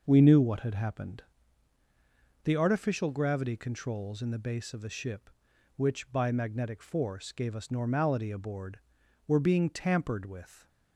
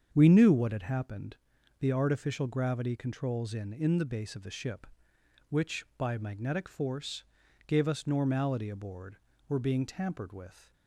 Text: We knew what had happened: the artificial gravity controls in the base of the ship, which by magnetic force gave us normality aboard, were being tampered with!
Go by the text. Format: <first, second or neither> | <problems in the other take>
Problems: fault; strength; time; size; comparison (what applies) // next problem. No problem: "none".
first | starts louder than the rest; strong; until 1.1 s; 7.5 dB // says "in" twice; at 3.7 s // pauses between "force" and "gave"; at 7.2 s; 0.42 s long